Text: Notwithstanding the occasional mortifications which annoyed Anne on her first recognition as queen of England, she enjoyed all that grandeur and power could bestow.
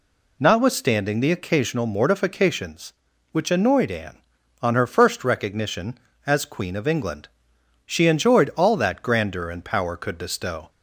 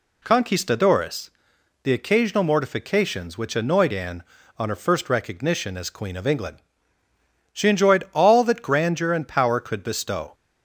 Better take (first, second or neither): first